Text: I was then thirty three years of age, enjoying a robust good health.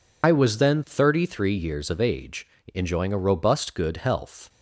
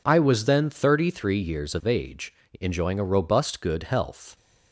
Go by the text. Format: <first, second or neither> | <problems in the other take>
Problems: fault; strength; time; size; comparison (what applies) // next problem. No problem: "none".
second | loses the start of "I"; at 0.2 s; 55 ms